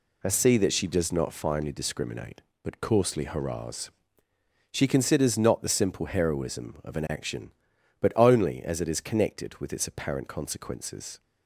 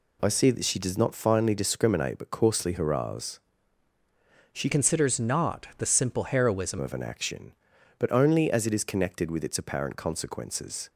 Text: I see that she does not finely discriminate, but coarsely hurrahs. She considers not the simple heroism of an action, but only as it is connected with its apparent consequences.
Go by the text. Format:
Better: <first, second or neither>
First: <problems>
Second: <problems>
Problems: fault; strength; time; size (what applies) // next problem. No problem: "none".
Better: first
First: none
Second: changes voice from "considers" to "heroism"; from 4.7 to 6.7 s; 2.0 s long